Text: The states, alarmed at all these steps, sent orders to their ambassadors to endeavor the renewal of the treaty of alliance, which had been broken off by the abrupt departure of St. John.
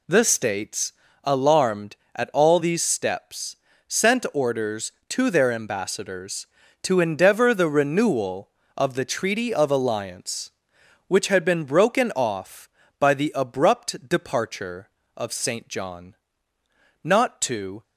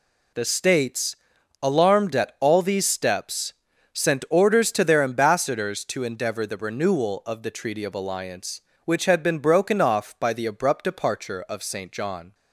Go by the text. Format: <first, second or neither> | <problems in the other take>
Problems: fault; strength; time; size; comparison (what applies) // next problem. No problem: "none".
second | goes on to say "Not to"; noticeable; from 17.0 s on; 0.80 s long